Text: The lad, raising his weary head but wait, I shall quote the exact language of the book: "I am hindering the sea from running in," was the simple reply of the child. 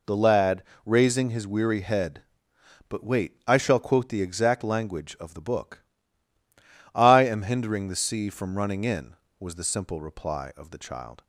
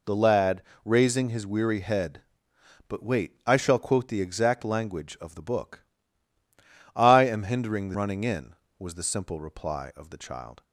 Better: first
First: none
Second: skips "sea from"; at 7.9 s

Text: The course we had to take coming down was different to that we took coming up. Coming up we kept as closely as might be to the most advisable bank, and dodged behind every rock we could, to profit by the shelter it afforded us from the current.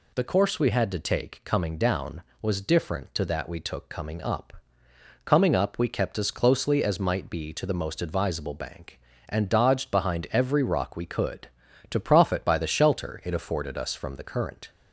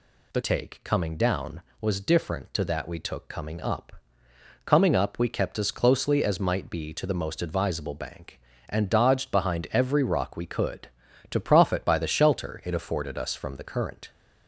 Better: first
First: none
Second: skips "course we had to"; at 0.4 s

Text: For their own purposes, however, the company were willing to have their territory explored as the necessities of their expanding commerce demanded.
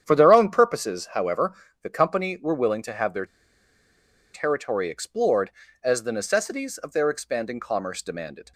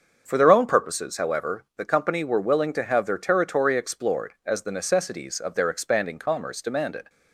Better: second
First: starts louder than the rest; strong; until 1.0 s; 9 dB // pauses between "their" and "territory"; at 3.2 s; 1.0 s long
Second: starts louder than the rest; until 1.2 s; 7 dB

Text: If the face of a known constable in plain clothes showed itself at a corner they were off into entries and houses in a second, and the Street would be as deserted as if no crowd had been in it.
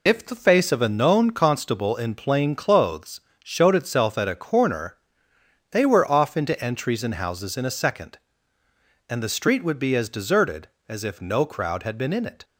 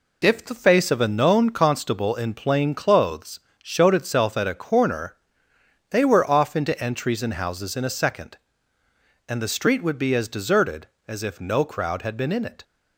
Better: second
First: loses the start of "If"; at 0.0 s; 30 ms // pauses between "clothes" and "showed"; slight; at 3.2 s; 0.20 s long // pauses between "corner" and "they"; noticeable; at 4.9 s; 0.72 s long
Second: pauses between "clothes" and "showed"; slight; at 3.4 s; 0.20 s long // pauses between "corner" and "they"; noticeable; at 5.1 s; 0.72 s long

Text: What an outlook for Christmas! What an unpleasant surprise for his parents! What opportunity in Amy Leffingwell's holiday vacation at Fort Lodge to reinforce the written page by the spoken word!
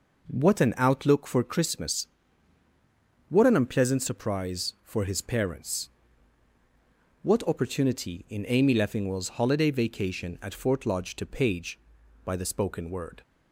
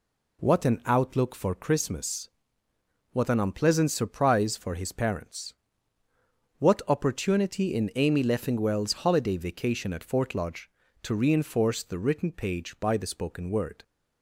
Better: second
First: skips "reinforce the written"; at 11.2 s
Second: none

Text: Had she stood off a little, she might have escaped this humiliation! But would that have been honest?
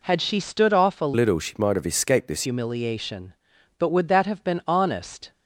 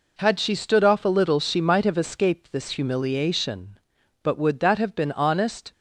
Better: second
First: changes voice from "little" to "this"; from 1.1 to 2.4 s; 1.3 s long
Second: none

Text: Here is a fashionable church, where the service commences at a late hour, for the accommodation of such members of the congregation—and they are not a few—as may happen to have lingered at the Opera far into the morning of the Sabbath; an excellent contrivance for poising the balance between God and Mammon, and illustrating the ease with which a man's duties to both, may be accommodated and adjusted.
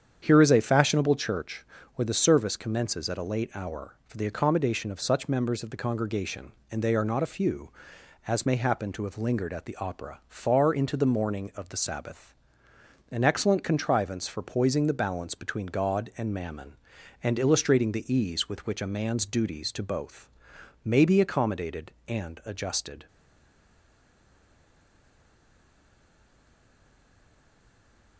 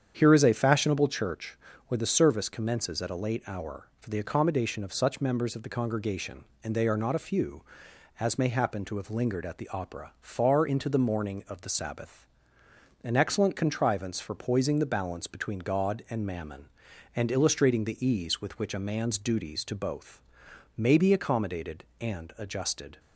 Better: second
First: starts louder than the rest; strong; until 1.2 s; 8 dB // stays silent after the last word; strong; from 23.0 s on; 5.1 s long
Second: starts louder than the rest; strong; until 1.1 s; 8 dB

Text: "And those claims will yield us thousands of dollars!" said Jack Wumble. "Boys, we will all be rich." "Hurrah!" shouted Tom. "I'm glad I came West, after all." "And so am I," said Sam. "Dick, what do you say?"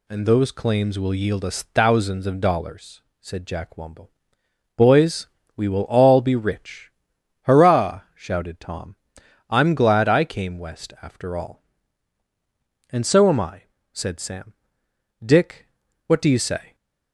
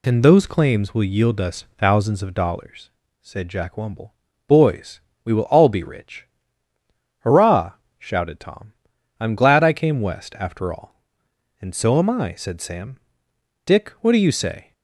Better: neither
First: none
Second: none

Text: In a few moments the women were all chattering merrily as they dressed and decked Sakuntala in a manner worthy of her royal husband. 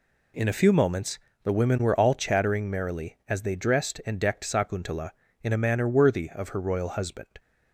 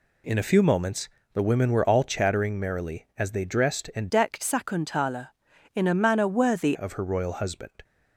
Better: first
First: pauses between "moments" and "the"; slight; at 1.1 s; 0.26 s long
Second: pauses between "moments" and "the"; slight; at 1.0 s; 0.26 s long // changes voice from "decked" to "worthy"; from 4.0 to 6.7 s; 2.7 s long

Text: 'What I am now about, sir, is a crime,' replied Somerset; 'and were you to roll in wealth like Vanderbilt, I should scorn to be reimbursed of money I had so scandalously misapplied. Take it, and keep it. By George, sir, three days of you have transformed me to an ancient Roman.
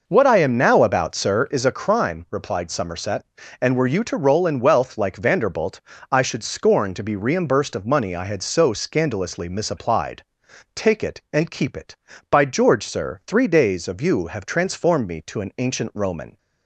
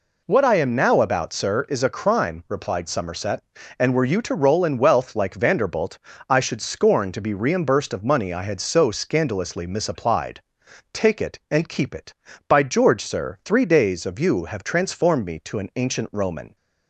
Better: second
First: starts louder than the rest; noticeable; until 1.8 s; 5.5 dB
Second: none

